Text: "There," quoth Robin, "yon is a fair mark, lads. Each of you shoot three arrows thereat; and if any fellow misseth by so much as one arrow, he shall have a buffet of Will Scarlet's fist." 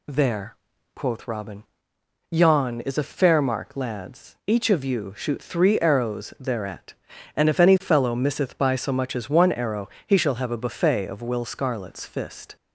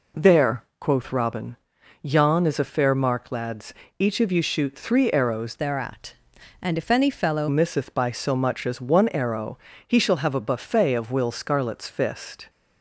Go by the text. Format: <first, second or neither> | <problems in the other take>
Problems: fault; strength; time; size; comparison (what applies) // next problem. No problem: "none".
first | changes voice from "thereat" to "fellow"; from 5.5 to 7.4 s; 1.9 s long